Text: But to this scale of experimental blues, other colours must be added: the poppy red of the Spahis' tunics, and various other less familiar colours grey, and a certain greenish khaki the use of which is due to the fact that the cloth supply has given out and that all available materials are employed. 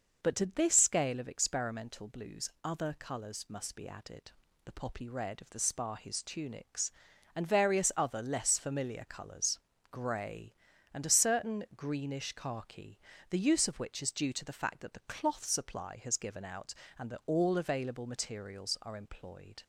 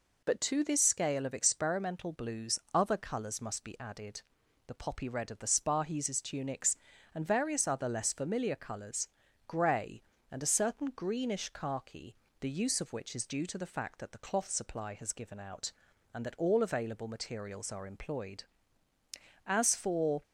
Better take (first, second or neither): first